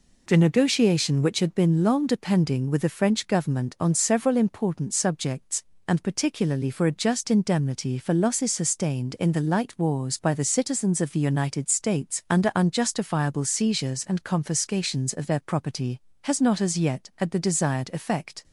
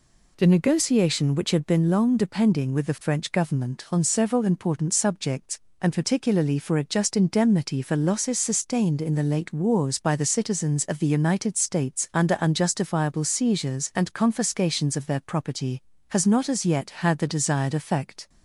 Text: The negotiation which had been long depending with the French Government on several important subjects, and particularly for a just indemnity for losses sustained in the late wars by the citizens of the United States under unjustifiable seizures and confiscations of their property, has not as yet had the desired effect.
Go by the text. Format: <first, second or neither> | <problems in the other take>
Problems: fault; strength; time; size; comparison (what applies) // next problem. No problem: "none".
second | says "light" for "late"; at 9.3 s